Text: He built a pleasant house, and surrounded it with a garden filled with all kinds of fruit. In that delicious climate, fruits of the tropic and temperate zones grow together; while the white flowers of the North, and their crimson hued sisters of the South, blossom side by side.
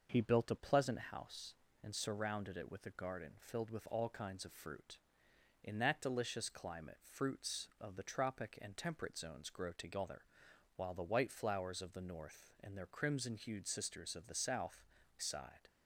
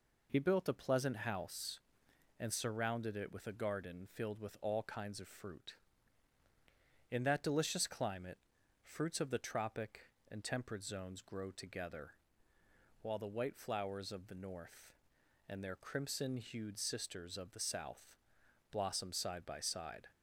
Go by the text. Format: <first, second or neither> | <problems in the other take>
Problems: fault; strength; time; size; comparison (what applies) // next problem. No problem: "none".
second | starts louder than the rest; noticeable; until 1.2 s; 6 dB // skips "blossom side by"; at 15.0 s